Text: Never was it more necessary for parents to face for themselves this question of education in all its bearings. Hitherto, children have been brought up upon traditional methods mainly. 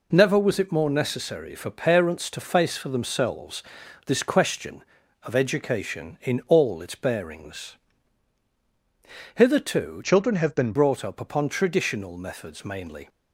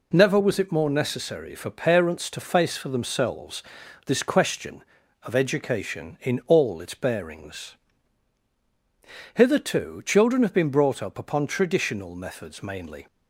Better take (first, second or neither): second